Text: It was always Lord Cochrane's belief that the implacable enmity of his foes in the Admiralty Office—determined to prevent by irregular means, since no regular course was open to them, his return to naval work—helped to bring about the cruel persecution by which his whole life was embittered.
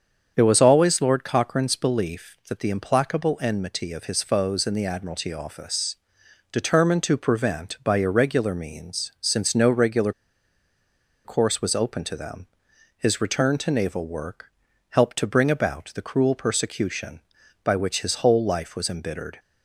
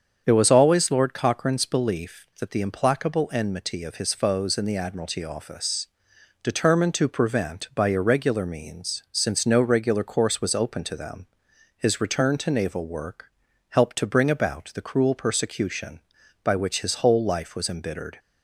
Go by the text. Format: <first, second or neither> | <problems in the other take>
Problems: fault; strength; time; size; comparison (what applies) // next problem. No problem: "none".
second | starts louder than the rest; strong; until 1.3 s; 7.5 dB; strong in the second // pauses between "regular" and "course"; at 10.1 s; 1.1 s long